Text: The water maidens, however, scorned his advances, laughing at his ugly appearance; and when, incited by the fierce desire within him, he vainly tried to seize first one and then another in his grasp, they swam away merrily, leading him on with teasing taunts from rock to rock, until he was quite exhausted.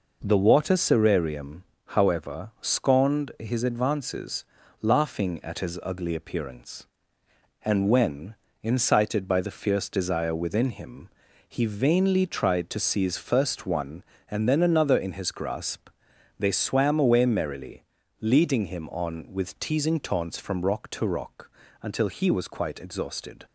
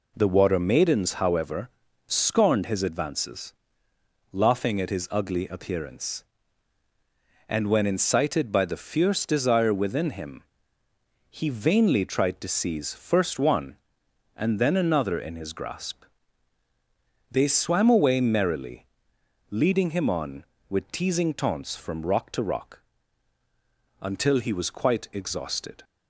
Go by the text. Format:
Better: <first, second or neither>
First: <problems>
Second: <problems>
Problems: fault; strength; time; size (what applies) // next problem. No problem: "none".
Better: second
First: says "serarium" for "maidens"; at 0.7 s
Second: none